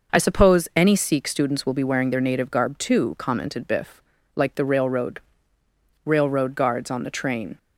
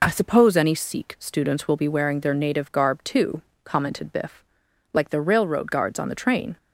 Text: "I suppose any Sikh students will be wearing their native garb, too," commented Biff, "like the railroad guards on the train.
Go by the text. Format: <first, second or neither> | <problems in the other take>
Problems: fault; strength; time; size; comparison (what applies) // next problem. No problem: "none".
second | says "railroad" twice; at 6.0 s